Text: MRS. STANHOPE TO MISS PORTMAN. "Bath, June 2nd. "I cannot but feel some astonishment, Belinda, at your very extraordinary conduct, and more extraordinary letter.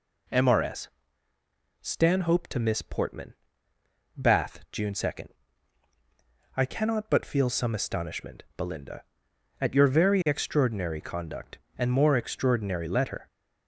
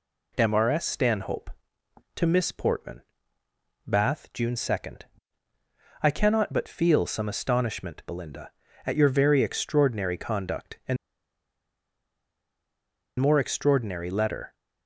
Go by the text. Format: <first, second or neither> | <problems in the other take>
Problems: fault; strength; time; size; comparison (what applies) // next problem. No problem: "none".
first | pauses between "and" and "more"; strong; at 10.9 s; 2.2 s long